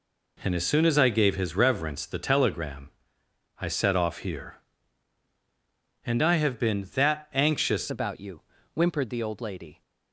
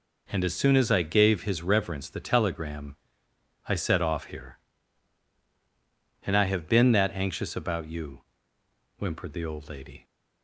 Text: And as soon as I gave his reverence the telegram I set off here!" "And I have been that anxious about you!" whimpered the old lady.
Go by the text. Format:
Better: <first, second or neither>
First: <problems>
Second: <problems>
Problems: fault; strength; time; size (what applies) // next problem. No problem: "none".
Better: second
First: pauses between "telegram" and "I"; noticeable; at 2.9 s; 0.70 s long // changes voice at "about"; from 7.9 s on; 1.9 s long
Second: pauses between "telegram" and "I"; noticeable; at 2.9 s; 0.72 s long